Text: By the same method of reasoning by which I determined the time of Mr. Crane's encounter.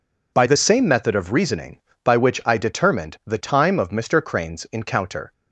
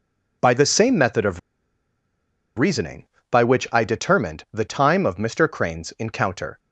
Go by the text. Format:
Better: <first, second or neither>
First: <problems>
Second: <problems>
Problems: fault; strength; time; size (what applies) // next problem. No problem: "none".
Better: first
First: none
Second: pauses between "of" and "reasoning"; at 1.3 s; 1.1 s long